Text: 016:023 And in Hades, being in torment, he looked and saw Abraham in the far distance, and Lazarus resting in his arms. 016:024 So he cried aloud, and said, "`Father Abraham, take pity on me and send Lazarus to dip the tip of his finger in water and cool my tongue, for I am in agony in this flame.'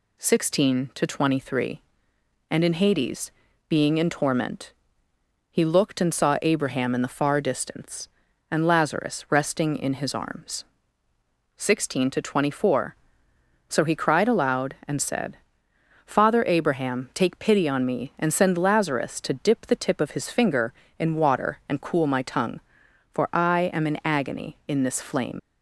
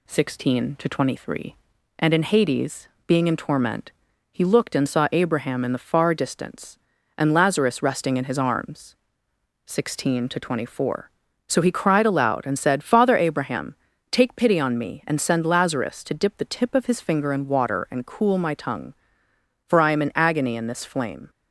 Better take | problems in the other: second | leaves "flame" unfinished; at 25.3 s; 60 ms

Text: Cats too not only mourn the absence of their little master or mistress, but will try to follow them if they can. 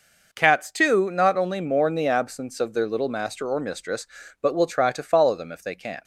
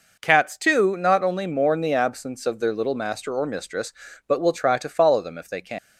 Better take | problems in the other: first | leaves "can" unfinished; at 5.7 s; 110 ms

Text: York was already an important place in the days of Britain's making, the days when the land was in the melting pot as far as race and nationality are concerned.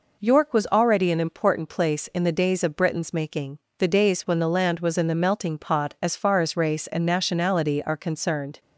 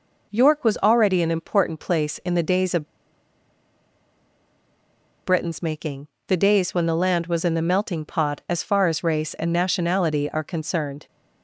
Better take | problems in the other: first | pauses between "of" and "Britain's"; strong; at 2.8 s; 2.3 s long

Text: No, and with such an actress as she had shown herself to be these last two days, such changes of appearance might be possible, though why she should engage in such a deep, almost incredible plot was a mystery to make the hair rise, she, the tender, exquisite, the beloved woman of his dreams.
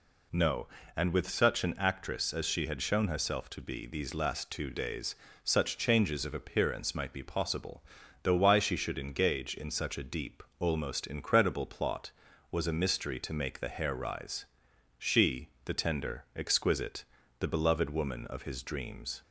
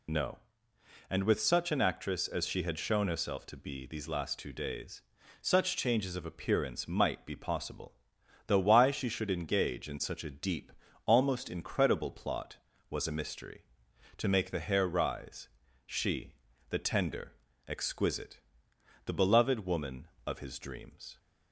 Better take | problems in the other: first | loses the start of "No"; at 0.0 s; 40 ms

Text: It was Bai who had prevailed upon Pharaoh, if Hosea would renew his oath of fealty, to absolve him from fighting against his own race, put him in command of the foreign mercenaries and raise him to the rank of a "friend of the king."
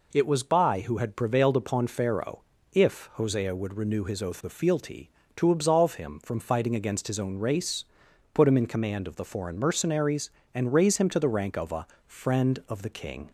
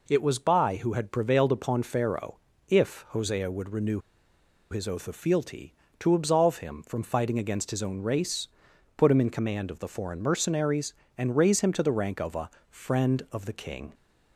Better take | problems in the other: first | pauses between "renew" and "his"; noticeable; at 3.9 s; 0.72 s long // pauses between "a" and "friend"; slight; at 12.4 s; 0.20 s long; slight in the first

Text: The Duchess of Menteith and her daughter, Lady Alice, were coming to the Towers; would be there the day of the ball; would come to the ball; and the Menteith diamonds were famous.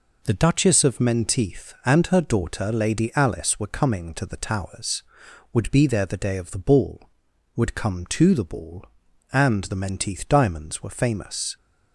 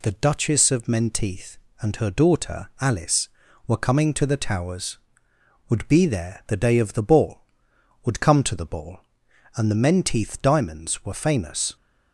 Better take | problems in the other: first | skips "Lady"; at 2.7 s

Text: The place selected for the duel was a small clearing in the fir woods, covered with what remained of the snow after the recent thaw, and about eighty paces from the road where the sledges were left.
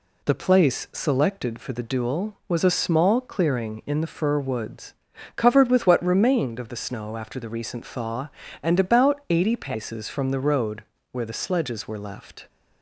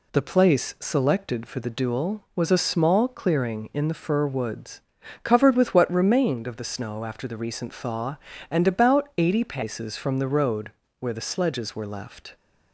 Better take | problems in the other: neither | pauses between "road" and "where"; slight; the same in both

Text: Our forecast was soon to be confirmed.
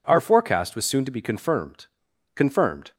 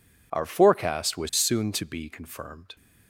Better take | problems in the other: second | says "confirmed" twice; at 2.3 s

